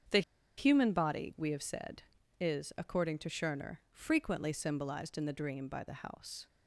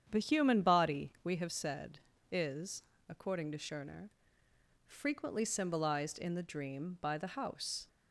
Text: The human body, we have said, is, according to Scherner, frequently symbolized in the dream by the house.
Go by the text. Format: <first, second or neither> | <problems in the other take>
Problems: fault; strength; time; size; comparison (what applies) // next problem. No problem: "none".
second | starts louder than the rest; strong; until 1.5 s; 7.5 dB; strong in the second // pauses between "The" and "human"; at 0.2 s; 0.36 s long